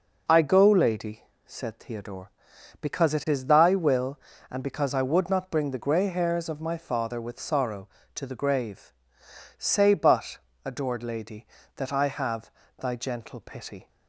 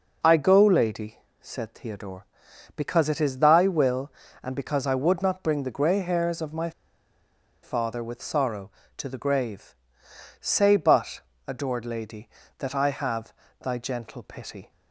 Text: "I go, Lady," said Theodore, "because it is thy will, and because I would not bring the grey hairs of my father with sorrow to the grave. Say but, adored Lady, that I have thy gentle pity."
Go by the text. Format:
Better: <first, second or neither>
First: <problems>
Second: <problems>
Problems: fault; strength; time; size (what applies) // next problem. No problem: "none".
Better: first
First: pauses between "have" and "thy"; slight; at 12.5 s; 0.26 s long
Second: pauses between "my" and "father"; noticeable; at 6.7 s; 0.92 s long // pauses between "have" and "thy"; slight; at 13.3 s; 0.26 s long